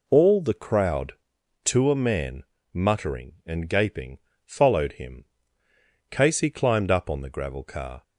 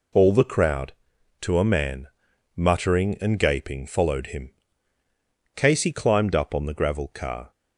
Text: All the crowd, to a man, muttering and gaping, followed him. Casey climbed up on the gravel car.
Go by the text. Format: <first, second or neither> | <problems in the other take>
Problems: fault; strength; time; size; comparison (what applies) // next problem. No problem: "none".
neither | none